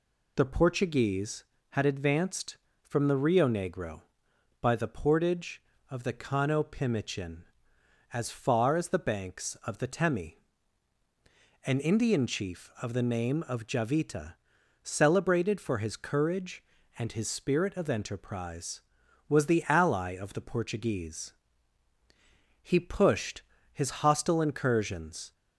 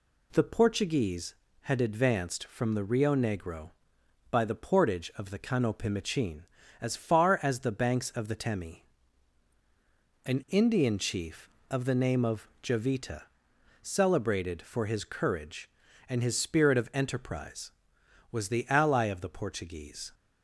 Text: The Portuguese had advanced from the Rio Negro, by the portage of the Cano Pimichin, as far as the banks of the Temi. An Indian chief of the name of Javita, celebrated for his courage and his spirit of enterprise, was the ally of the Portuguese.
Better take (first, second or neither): second